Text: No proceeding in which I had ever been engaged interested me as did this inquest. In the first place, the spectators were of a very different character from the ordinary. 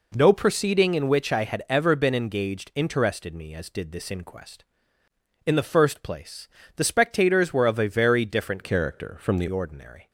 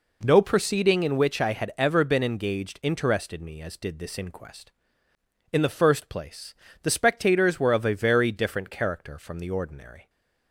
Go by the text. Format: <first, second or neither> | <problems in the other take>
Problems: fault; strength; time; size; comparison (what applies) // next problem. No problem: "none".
second | changes voice from "character" to "the"; from 8.6 to 9.4 s; 0.8 s long